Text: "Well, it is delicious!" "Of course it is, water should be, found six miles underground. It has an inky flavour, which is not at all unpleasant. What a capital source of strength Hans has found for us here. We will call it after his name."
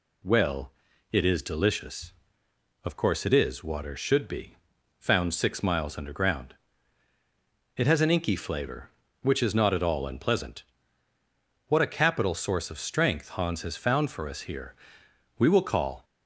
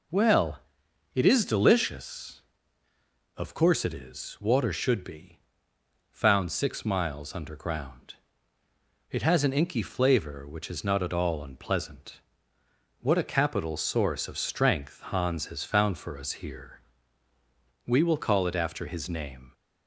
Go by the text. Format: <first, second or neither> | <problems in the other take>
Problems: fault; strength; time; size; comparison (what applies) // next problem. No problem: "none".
second | stops before "it after his name"; at 16.0 s